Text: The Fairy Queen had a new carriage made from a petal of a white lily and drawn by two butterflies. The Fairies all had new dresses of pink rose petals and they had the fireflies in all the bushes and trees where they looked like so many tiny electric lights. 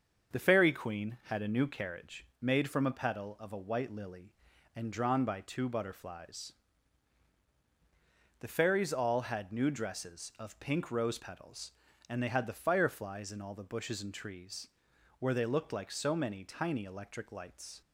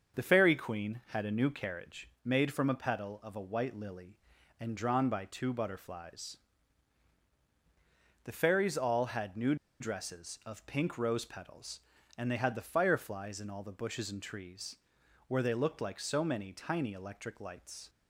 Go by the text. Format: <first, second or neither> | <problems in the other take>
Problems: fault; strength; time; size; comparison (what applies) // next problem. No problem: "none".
first | starts louder than the rest; until 1.2 s; 6.5 dB; also in the first // pauses between "new" and "dresses"; slight; at 9.5 s; 0.25 s long // pauses between "trees" and "where"; noticeable; at 14.7 s; 0.52 s long; noticeable in the first